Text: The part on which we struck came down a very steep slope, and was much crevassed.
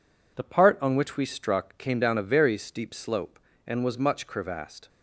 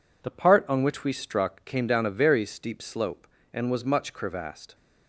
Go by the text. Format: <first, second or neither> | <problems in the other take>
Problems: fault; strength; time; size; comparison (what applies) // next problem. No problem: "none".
neither | none